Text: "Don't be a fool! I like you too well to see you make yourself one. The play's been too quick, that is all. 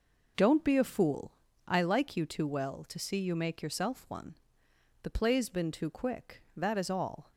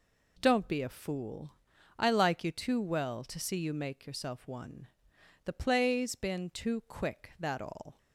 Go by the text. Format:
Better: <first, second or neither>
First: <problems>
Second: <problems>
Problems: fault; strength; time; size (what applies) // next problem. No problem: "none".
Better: first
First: none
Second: skips "is"; at 7.5 s